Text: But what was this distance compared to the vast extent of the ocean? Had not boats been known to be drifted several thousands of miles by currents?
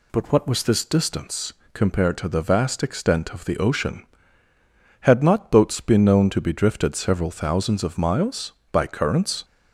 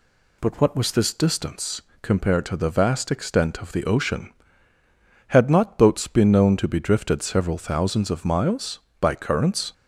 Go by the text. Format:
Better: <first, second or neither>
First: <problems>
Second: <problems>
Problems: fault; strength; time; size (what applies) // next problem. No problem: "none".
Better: neither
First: pauses between "distance" and "compared"; slight; at 1.5 s; 0.20 s long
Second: pauses between "distance" and "compared"; slight; at 1.8 s; 0.20 s long